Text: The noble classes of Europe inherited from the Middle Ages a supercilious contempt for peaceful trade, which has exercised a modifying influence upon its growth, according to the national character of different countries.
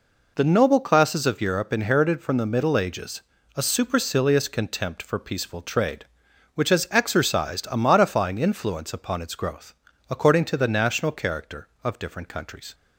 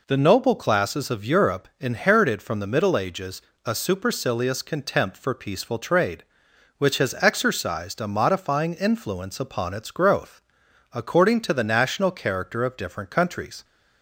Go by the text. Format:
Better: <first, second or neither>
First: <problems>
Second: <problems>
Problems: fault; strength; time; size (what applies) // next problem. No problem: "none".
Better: neither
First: pauses between "Ages" and "a"; slight; at 3.2 s; 0.32 s long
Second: pauses between "Ages" and "a"; slight; at 3.3 s; 0.24 s long